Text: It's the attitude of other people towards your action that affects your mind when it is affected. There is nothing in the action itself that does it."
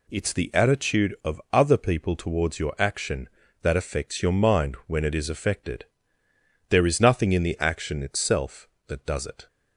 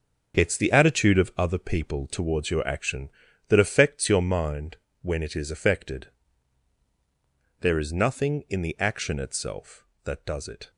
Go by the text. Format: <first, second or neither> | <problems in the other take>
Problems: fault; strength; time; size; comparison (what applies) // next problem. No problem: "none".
first | gets quieter; strong; throughout; 9.5 dB // pauses between "mind" and "when"; slight; at 4.7 s; 0.26 s long